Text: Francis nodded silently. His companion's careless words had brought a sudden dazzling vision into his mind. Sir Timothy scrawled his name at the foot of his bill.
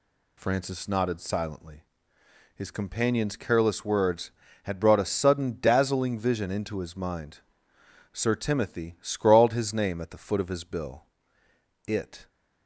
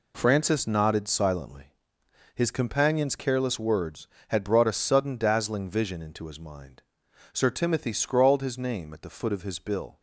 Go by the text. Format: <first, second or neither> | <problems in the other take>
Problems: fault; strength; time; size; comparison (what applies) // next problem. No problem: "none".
second | goes on to say "It"; slight; from 11.8 s on; 0.42 s long